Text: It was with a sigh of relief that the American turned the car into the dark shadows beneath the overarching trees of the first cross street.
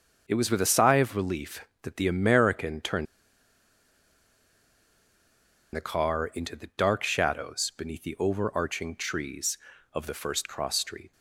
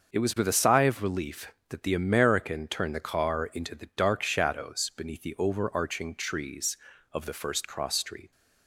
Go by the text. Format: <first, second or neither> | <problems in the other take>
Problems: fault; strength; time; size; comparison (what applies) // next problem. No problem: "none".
second | starts louder than the rest; until 1.2 s; 6.5 dB; also in the second // pauses between "turned" and "the"; strong; at 3.0 s; 2.7 s long